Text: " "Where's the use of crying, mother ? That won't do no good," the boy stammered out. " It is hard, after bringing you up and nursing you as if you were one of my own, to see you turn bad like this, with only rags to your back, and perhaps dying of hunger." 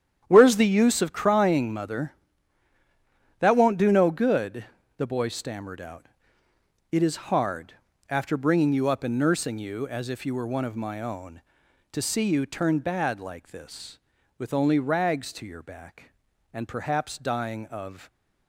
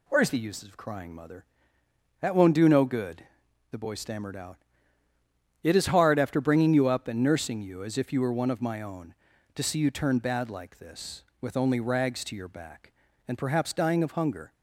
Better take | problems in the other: second | starts louder than the rest; strong; until 1.2 s; 9 dB // stops before "hunger"; at 18.0 s

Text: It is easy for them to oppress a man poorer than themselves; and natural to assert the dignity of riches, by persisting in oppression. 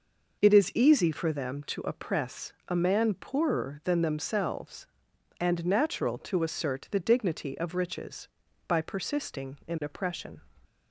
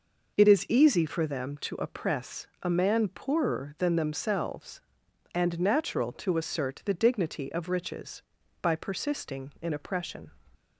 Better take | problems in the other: neither | pauses between "oppress" and "a"; slight; the same in both

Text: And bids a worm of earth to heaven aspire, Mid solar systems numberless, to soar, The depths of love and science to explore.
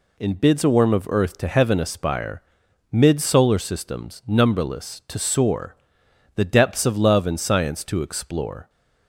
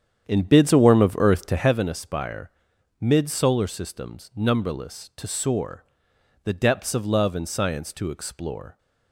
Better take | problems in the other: first | starts louder than the rest; strong; until 1.8 s; 8.5 dB

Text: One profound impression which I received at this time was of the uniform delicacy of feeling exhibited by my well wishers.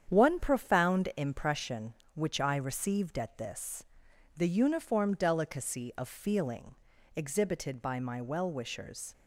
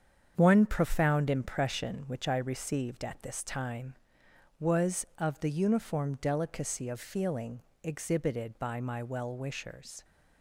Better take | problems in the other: second | starts louder than the rest; strong; until 1.0 s; 8.5 dB; strong in the second // skips "time was of"; at 4.1 s // pauses between "feeling" and "exhibited"; at 6.7 s; 0.40 s long; slight in the second

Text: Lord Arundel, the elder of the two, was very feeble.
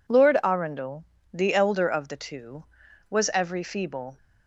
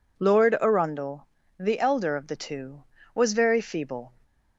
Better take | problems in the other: second | says "every" for "very"; at 3.3 s

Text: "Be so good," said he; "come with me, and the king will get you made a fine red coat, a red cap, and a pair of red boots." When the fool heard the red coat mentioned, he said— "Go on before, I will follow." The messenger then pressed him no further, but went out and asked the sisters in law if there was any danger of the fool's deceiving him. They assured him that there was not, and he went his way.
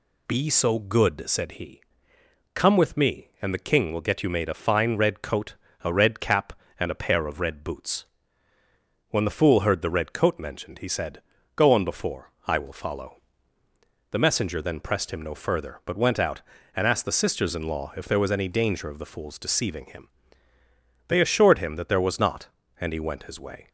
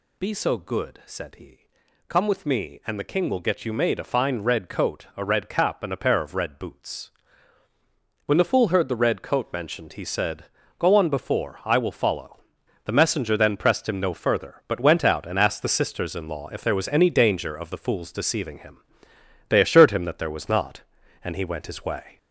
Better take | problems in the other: first | gets louder; noticeable; throughout; 4.5 dB

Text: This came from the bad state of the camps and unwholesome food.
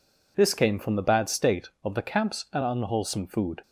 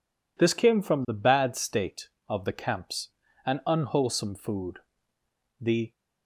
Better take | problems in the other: first | goes on to say "The"; slight; from 5.5 s on; 0.32 s long

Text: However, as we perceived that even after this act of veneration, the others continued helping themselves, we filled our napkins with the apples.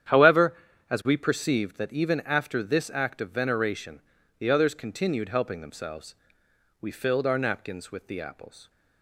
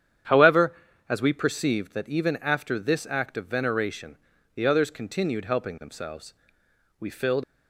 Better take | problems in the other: first | starts louder than the rest; strong; until 1.6 s; 9 dB; strong in the first // stops before "our napkins with the apples"; at 7.4 s

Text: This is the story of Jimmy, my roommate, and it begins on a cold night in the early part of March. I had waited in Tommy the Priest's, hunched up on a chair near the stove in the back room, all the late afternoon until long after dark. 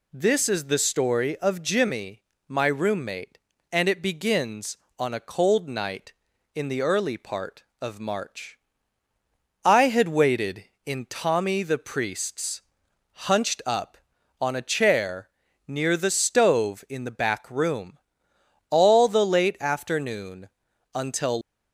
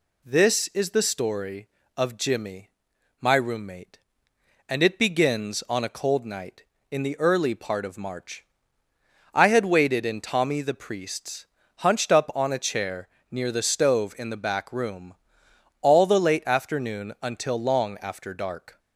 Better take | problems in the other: second | pauses between "chair" and "near"; at 15.2 s; 0.40 s long; slight in the second // pauses between "afternoon" and "until"; at 20.4 s; 0.44 s long // stops before "long after dark"; at 21.4 s

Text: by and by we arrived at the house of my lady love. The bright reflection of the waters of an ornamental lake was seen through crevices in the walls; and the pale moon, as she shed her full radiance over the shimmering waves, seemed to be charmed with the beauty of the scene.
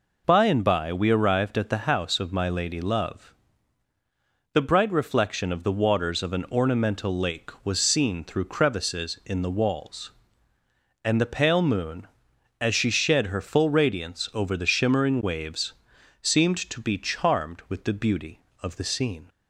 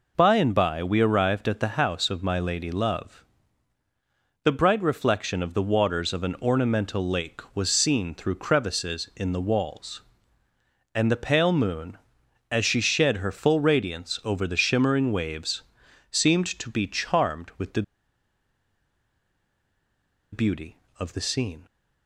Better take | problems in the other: first | pauses between "the" and "beauty"; strong; at 17.8 s; 2.5 s long

